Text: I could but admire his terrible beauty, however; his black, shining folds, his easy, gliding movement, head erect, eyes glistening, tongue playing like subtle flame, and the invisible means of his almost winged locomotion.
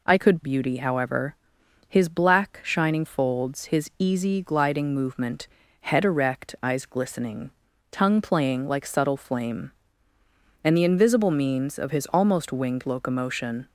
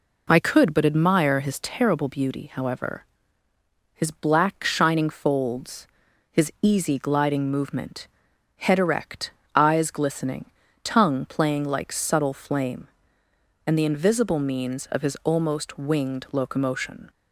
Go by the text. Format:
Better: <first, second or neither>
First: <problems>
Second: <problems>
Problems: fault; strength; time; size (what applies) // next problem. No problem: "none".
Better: second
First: skips "but admire his terrible"; at 0.4 s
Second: none